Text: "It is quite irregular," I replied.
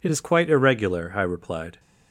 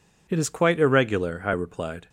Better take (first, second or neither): neither